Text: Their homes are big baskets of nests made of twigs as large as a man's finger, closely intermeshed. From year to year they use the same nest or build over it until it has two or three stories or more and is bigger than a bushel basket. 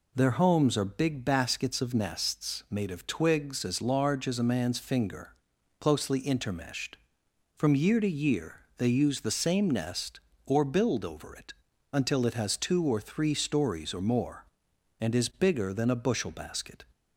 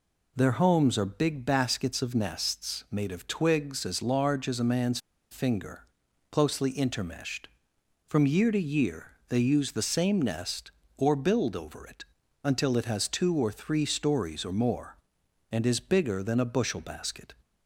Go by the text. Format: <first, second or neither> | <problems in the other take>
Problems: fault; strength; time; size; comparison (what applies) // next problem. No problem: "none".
first | pauses between "man's" and "finger"; slight; at 4.9 s; 0.33 s long // pauses between "year" and "they"; slight; at 9.0 s; 0.20 s long; slight in the first // pauses between "it" and "until"; at 12.0 s; 0.38 s long; also in the first